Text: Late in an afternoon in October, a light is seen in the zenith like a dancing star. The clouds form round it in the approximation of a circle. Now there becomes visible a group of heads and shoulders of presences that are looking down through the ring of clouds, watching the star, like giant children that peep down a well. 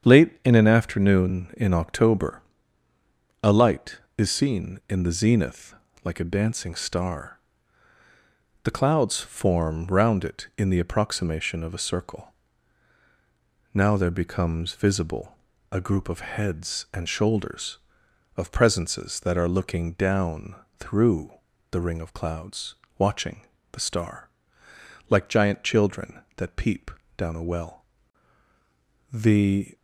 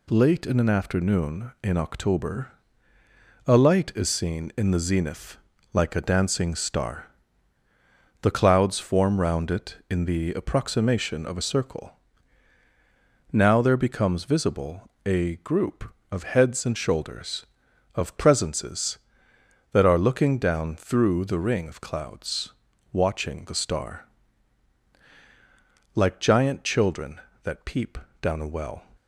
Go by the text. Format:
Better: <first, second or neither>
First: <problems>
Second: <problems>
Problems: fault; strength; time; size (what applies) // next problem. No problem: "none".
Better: second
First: starts louder than the rest; strong; until 1.1 s; 8 dB // pauses between "zenith" and "like"; slight; at 5.7 s; 0.28 s long // pauses between "visible" and "a"; slight; at 15.3 s; 0.34 s long // pauses between "down" and "through"; slight; at 20.5 s; 0.24 s long // pauses between "through" and "the"; at 21.3 s; 0.40 s long // pauses between "watching" and "the"; slight; at 23.4 s; 0.28 s long // pauses between "peep" and "down"; slight; at 26.9 s; 0.26 s long // goes on to say "The"; noticeable; from 29.1 s on; 0.64 s long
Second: pauses between "zenith" and "like"; at 5.3 s; 0.38 s long // pauses between "visible" and "a"; slight; at 14.8 s; 0.16 s long // pauses between "peep" and "down"; slight; at 27.9 s; 0.24 s long